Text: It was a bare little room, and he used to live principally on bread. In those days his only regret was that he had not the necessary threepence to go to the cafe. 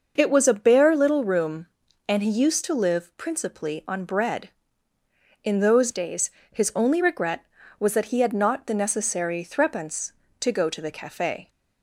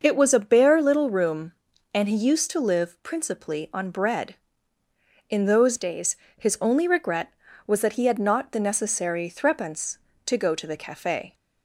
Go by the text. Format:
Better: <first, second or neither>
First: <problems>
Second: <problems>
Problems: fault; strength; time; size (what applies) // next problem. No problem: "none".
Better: neither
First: starts louder than the rest; noticeable; until 1.1 s; 6 dB // pauses between "days" and "his"; slight; at 6.3 s; 0.20 s long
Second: starts louder than the rest; noticeable; until 1.0 s; 6 dB // pauses between "days" and "his"; slight; at 6.1 s; 0.20 s long